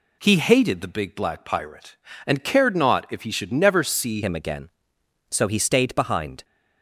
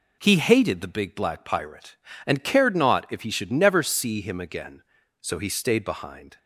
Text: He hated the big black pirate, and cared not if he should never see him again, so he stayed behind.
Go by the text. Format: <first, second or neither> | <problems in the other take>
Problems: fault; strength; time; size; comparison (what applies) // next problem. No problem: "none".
second | changes voice at "him"; from 4.2 s on; 2.2 s long